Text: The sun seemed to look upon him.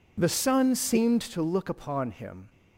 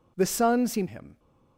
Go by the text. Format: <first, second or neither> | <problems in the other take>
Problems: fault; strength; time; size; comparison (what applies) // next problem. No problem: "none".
first | skips "to look upon"; at 0.8 s